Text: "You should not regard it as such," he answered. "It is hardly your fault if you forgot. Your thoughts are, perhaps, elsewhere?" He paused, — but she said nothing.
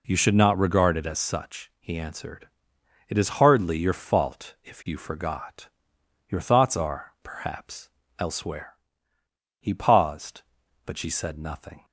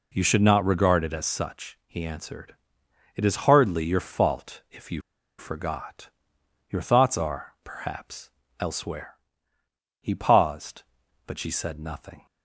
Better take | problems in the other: first | pauses between "you" and "forgot"; at 5.0 s; 0.37 s long

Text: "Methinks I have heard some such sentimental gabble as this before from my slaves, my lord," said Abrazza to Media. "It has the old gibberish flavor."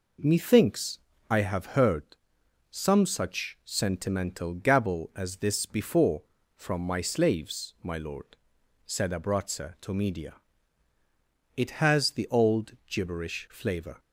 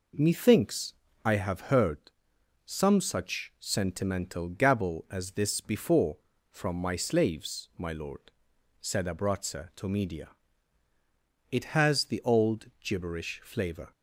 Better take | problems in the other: neither | pauses between "Methinks" and "I"; slight; the same in both // pauses between "heard" and "some"; noticeable; the same in both

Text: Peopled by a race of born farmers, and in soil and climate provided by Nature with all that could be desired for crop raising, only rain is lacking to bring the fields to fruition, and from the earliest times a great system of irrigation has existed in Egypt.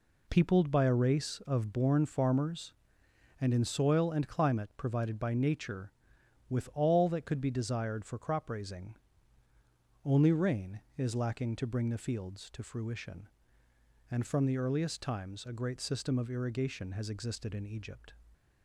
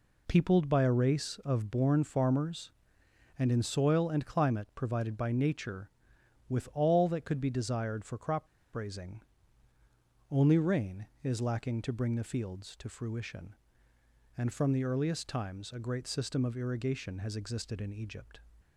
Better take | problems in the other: first | pauses between "crop" and "raising"; slight; at 8.4 s; 0.27 s long

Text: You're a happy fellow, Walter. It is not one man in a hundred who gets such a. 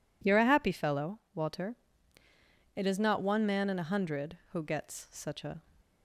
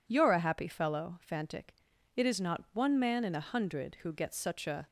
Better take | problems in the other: first | says "Fantic" for "Walter"; at 1.2 s

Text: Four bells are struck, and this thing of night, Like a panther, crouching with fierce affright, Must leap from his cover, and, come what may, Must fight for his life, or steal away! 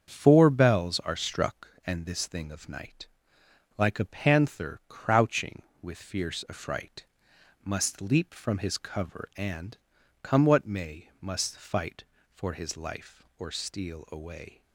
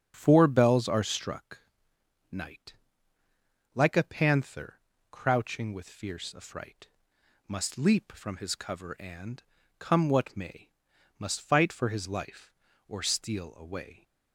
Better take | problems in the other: first | starts louder than the rest; strong; until 1.1 s; 7 dB; also in the first // skips "and this thing of"; at 1.9 s

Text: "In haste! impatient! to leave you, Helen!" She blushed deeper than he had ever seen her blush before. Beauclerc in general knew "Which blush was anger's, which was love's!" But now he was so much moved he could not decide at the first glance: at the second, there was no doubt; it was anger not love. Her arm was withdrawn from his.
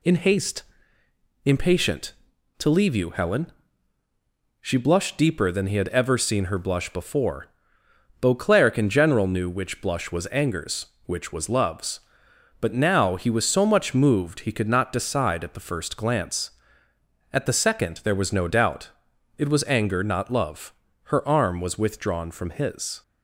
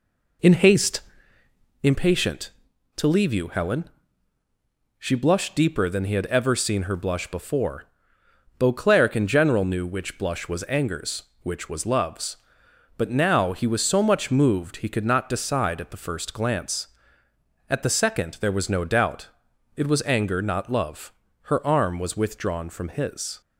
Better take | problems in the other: first | starts louder than the rest; until 1.9 s; 4 dB

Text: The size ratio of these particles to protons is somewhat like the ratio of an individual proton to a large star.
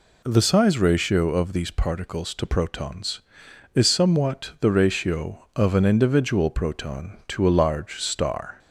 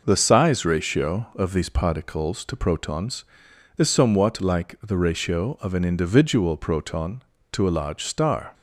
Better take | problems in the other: second | skips "like"; at 4.5 s

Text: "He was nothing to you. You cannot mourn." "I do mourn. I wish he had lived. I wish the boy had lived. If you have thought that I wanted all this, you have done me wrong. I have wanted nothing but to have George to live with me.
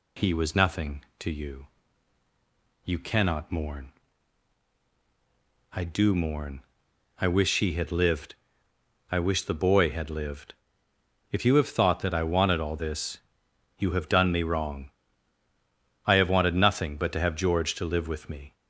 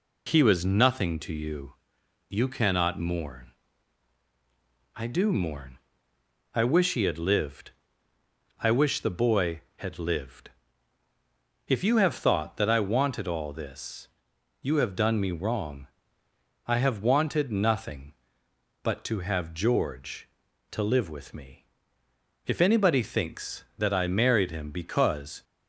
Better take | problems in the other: first | goes on to say "If anybody thinks that I married him because"; strong; from 22.4 s on; 2.9 s long

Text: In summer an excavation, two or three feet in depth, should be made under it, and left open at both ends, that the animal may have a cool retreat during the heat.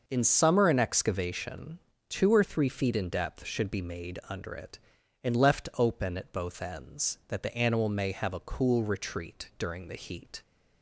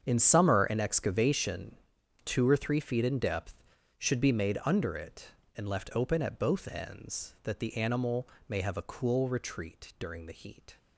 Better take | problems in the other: first | gets quieter; strong; throughout; 14.5 dB // starts louder than the rest; strong; until 1.0 s; 7.5 dB; noticeable in the first // pauses between "animal" and "may"; slight; at 8.2 s; 0.20 s long

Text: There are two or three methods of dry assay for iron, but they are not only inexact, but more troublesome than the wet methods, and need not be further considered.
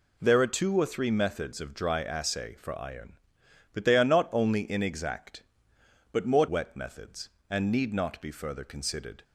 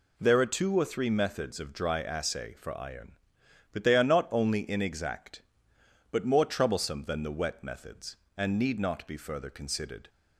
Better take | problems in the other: second | skips "troublesome than the"; at 6.4 s

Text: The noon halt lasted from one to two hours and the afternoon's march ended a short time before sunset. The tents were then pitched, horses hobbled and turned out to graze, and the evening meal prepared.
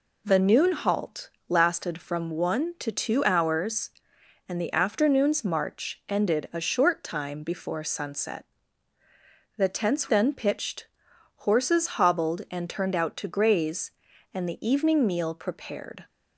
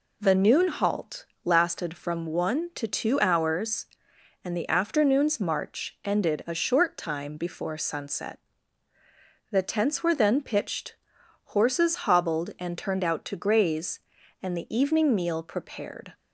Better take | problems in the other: second | pauses between "halt" and "lasted"; slight; at 1.2 s; 0.18 s long; slight in the second // skips "were"; at 10.0 s

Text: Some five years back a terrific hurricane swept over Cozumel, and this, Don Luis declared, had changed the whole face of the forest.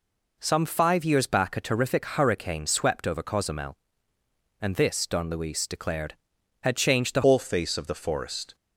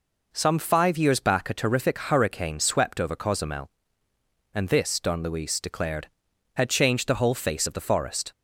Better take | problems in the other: second | changes voice at "whole"; from 7.2 s on; 1.3 s long

